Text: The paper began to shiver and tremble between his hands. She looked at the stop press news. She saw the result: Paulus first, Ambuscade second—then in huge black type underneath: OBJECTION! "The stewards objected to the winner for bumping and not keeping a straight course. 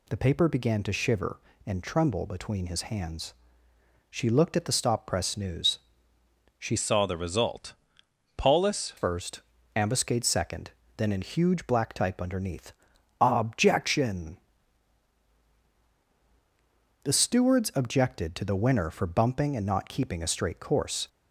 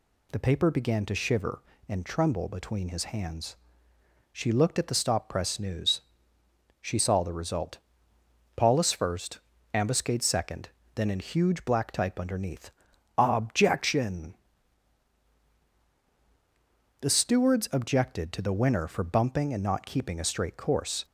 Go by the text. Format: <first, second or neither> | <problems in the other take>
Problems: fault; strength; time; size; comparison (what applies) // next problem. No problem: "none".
second | changes voice from "saw" to "Paulus"; from 6.7 to 8.9 s; 2.2 s long